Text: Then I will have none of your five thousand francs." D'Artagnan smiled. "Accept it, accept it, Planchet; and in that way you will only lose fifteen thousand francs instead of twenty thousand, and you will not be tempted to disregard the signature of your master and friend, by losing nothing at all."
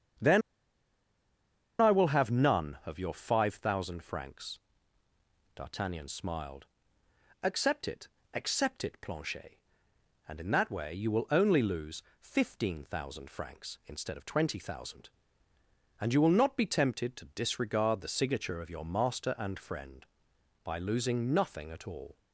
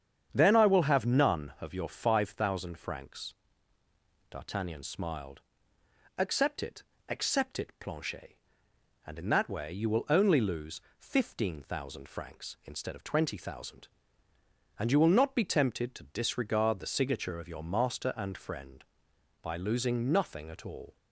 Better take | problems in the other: second | starts louder than the rest; strong; until 2.5 s; 8 dB; strong in the second // pauses between "Then" and "I"; strong; at 0.4 s; 1.3 s long // pauses between "lose" and "fifteen"; slight; at 12.0 s; 0.18 s long; slight in the second

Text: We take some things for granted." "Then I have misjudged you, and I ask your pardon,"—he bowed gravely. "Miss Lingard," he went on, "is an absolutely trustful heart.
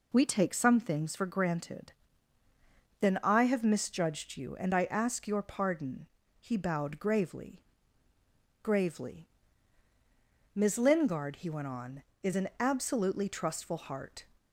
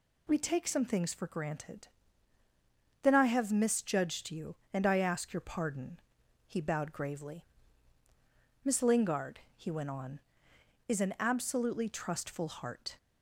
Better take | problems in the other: second | says "gravely" twice; at 8.6 s

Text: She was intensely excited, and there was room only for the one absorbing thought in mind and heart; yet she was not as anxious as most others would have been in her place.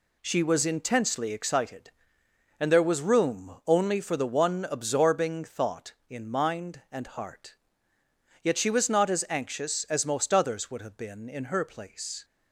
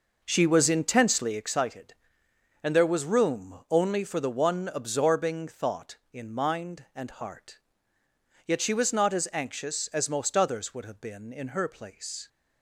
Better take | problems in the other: first | starts louder than the rest; noticeable; until 1.5 s; 5.5 dB

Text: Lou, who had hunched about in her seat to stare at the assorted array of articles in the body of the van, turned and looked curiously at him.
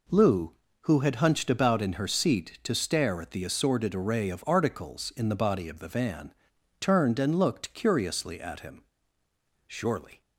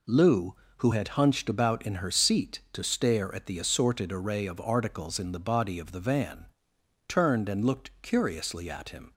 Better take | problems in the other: second | goes on to say "Surely"; from 9.6 s on; 0.54 s long

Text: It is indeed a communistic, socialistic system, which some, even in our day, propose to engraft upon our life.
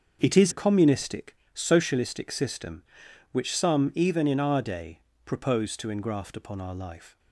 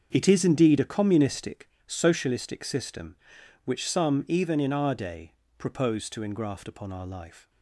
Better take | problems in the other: second | starts louder than the rest; until 1.2 s; 6.5 dB; also in the second // skips "indeed"; at 0.5 s

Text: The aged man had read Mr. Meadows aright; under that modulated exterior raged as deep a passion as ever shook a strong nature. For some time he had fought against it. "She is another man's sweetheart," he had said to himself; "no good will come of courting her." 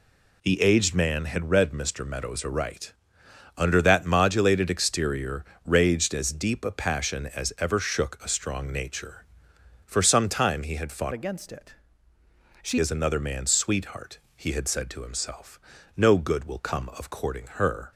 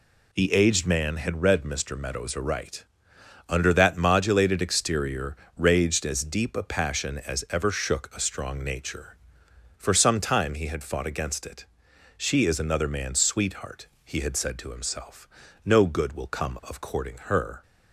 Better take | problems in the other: second | pauses between "exterior" and "raged"; slight; at 5.4 s; 0.22 s long; slight in the second // changes voice from "against" to "She"; from 11.1 to 12.7 s; 1.6 s long

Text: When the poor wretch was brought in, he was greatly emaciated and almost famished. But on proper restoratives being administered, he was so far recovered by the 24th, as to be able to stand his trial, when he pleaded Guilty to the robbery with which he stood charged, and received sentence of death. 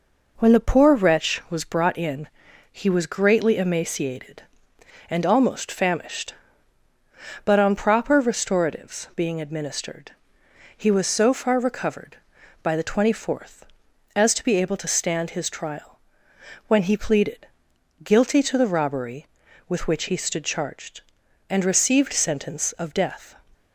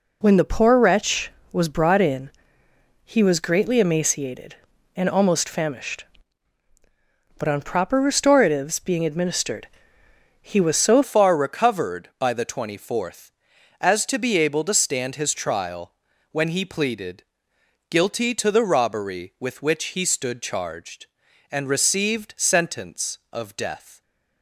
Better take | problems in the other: first | changes voice at "far"; from 11.0 s on; 13.0 s long // pauses between "pleaded" and "Guilty"; noticeable; at 17.2 s; 0.66 s long; noticeable in the first

